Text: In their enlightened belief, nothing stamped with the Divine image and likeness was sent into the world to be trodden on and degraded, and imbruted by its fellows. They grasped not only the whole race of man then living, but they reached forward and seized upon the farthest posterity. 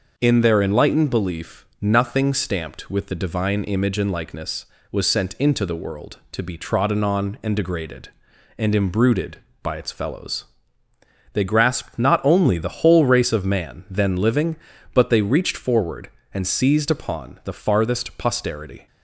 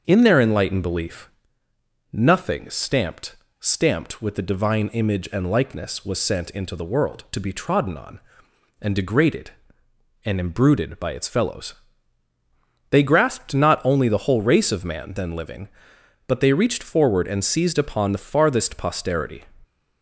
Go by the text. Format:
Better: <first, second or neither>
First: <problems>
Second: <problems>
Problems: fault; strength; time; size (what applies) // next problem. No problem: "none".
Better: first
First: none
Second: starts louder than the rest; until 1.0 s; 6.5 dB // says "stamped" twice; at 3.5 s